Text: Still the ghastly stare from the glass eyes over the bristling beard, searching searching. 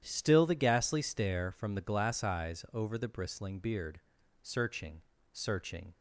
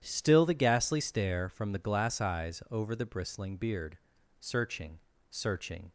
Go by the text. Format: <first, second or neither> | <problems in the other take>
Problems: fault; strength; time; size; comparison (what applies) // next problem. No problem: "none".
neither | starts louder than the rest; strong; the same in both // pauses between "searching" and "searching"; slight; the same in both